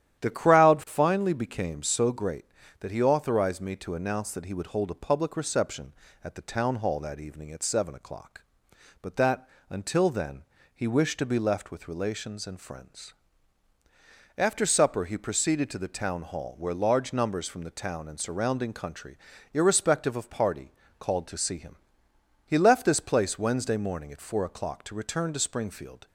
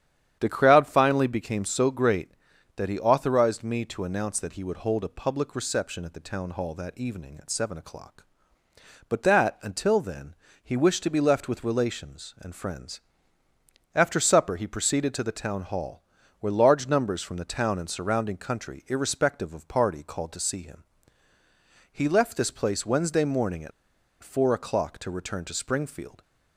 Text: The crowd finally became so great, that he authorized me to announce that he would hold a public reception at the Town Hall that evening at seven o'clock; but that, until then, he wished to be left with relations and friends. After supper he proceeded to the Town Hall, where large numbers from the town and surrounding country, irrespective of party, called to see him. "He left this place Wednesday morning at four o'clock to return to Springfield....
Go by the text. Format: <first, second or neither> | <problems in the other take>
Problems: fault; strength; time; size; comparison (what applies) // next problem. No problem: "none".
first | starts louder than the rest; strong; until 1.4 s; 9.5 dB; strong in the first // pauses between "at" and "four"; noticeable; at 23.7 s; 0.52 s long